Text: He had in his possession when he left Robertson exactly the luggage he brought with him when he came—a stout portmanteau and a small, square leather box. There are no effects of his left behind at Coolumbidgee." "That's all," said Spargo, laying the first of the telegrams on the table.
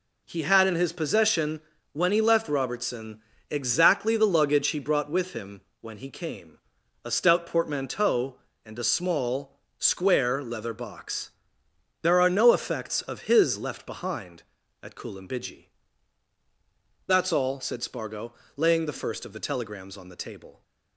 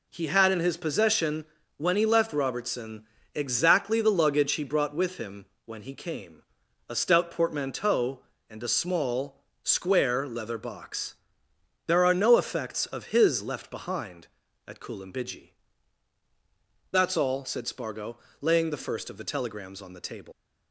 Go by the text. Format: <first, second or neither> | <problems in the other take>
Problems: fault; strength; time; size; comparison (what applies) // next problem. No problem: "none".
first | pauses between "possession" and "when"; slight; at 1.4 s; 0.32 s long; slight in the first // pauses between "Robertson" and "exactly"; slight; at 3.0 s; 0.30 s long; slight in the first // pauses between "him" and "when"; slight; at 5.4 s; 0.20 s long; slight in the first // leaves "table" unfinished; at 20.3 s; 150 ms